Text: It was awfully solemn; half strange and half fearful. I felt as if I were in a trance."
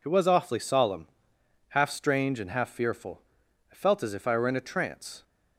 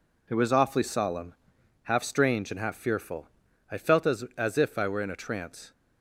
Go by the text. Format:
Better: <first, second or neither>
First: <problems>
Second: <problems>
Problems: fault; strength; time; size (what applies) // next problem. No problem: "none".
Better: first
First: none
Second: says "as" twice; at 4.3 s